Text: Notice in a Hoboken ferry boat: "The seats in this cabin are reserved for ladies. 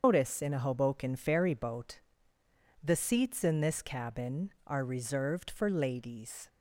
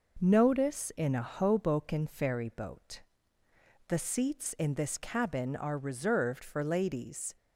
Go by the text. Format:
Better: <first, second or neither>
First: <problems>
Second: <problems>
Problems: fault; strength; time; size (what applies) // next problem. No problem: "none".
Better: second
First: loses the start of "Notice"; at 0.0 s; 135 ms // starts louder than the rest; until 1.0 s; 7 dB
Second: none